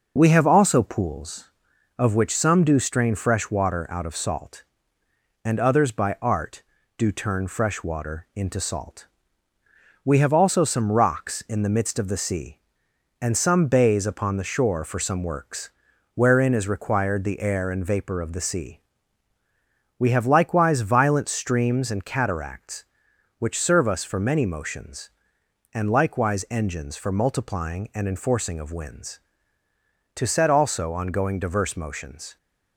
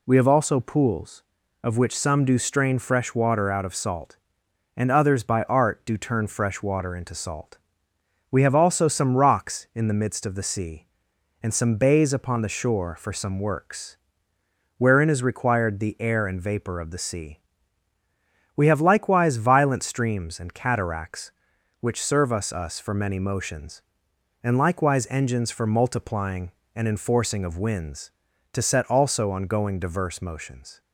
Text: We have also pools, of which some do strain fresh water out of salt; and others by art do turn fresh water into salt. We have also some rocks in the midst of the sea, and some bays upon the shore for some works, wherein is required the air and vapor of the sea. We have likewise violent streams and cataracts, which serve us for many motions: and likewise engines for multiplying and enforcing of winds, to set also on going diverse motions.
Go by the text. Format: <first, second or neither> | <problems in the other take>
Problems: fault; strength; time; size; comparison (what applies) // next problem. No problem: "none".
first | says "us" twice; at 22.5 s